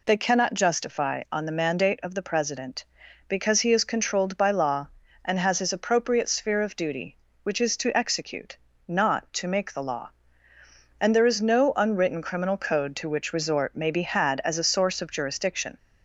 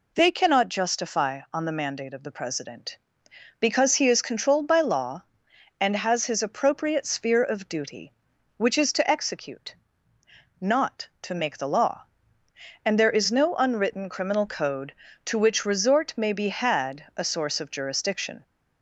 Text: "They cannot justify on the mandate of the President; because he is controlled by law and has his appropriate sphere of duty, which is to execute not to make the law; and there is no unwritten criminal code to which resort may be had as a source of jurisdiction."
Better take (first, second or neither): first